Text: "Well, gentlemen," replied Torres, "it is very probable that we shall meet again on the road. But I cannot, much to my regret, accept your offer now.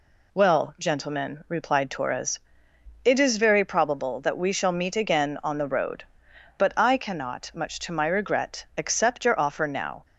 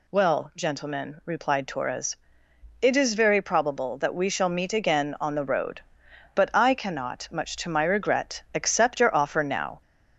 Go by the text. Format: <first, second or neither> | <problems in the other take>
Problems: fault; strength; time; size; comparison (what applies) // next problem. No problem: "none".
first | gets louder; slight; throughout; 2.5 dB